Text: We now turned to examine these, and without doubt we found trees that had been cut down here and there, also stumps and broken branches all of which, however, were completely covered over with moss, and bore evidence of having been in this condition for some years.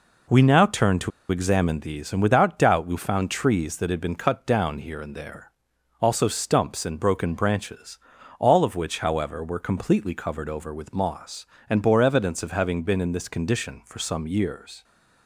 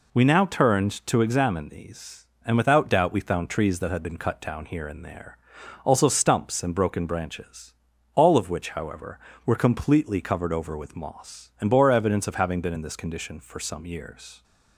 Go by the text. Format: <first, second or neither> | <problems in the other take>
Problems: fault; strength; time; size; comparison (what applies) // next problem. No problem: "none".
second | pauses between "to" and "examine"; slight; at 1.1 s; 0.21 s long // pauses between "branches" and "all"; at 7.9 s; 0.42 s long; also in the second